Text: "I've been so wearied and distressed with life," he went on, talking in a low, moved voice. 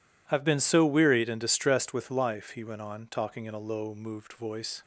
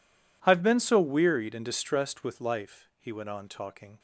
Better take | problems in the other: first | stops before "in a low moved voice"; at 3.9 s

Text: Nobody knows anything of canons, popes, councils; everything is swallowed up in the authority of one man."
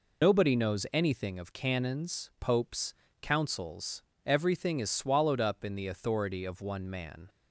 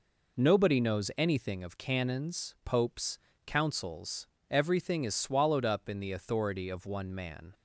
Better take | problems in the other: second | loses the start of "Nobody"; at 0.2 s; 100 ms

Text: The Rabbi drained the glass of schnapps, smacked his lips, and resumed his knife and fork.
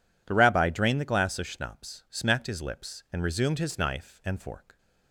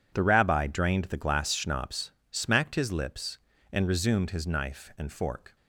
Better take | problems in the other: first | skips "of"; at 1.5 s

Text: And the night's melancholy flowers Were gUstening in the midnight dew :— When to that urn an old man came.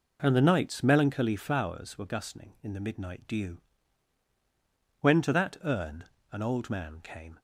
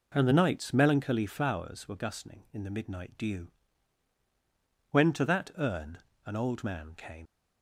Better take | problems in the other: first | pauses between "urn" and "an"; slight; at 5.9 s; 0.26 s long; slight in the first // leaves "came" unfinished; at 7.2 s; 75 ms

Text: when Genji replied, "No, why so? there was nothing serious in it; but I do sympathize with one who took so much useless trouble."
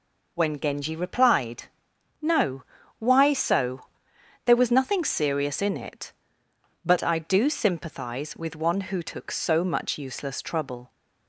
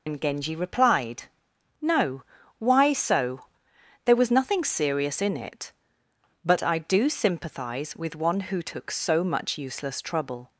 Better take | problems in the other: first | loses the start of "when"; at 0.0 s; 120 ms

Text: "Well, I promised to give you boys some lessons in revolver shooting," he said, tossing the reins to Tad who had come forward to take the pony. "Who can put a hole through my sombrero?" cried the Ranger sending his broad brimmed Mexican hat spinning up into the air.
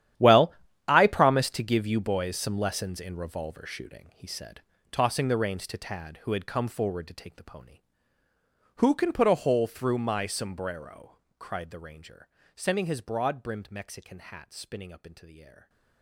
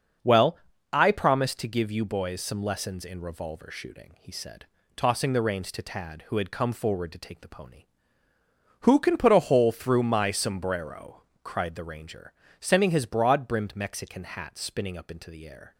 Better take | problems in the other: second | gets quieter; strong; throughout; 16 dB // starts louder than the rest; strong; until 1.5 s; 11 dB; also in the second // pauses between "Ranger" and "sending"; slight; at 12.2 s; 0.26 s long; slight in the second

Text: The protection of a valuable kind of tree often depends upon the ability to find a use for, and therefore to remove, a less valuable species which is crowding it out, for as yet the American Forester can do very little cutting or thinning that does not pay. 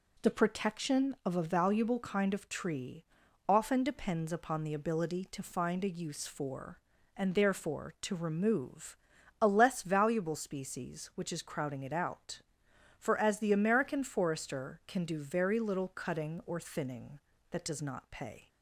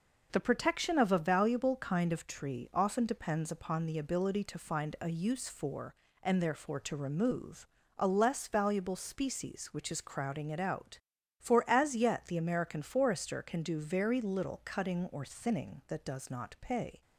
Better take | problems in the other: second | pauses between "tree" and "often"; at 3.0 s; 0.44 s long // skips "yet"; at 13.3 s

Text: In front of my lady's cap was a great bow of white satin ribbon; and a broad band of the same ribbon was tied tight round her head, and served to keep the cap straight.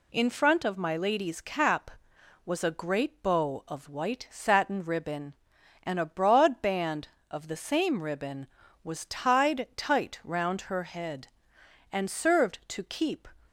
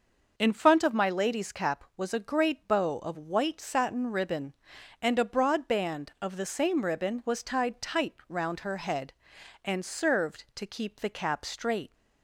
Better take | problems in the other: second | stops before "the cap straight"; at 13.4 s

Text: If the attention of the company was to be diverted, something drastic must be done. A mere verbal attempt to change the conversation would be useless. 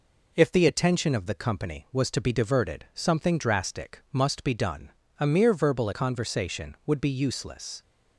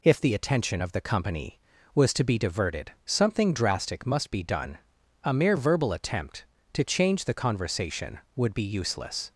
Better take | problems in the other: second | skips "attempt to change the"; at 5.9 s

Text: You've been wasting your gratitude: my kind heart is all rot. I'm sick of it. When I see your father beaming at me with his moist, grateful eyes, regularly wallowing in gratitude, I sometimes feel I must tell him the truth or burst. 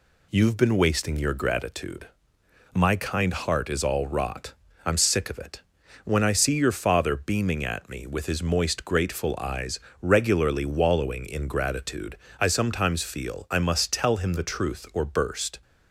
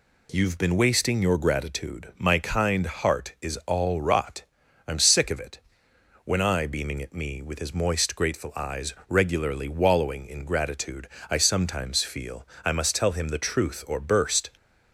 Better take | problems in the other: first | skips "see your father"; at 6.6 s // pauses between "feel" and "I"; slight; at 12.4 s; 0.18 s long

